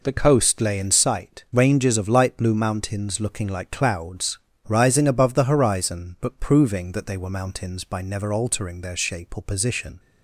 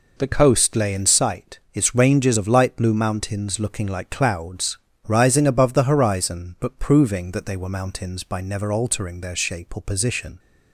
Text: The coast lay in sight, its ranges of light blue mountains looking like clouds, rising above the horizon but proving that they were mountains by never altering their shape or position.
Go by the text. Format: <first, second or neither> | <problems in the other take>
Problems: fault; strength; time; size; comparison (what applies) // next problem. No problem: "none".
second | skips "its"; at 1.4 s